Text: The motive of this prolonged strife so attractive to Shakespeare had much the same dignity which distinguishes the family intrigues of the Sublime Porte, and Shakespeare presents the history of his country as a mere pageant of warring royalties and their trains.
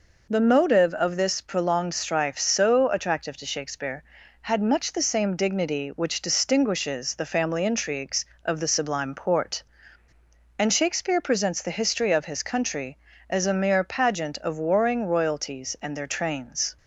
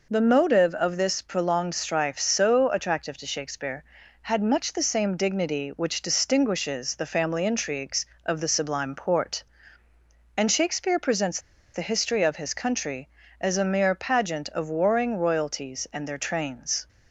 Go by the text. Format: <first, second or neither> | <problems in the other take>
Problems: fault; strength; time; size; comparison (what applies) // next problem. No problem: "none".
first | pauses between "presents" and "the"; slight; at 11.3 s; 0.34 s long